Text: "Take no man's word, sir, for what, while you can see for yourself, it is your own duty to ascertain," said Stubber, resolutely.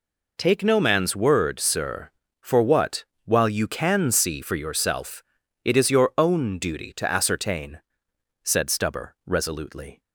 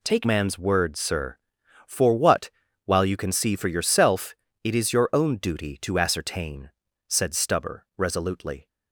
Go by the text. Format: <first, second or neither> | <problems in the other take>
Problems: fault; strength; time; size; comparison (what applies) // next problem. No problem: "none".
first | skips "no"; at 0.2 s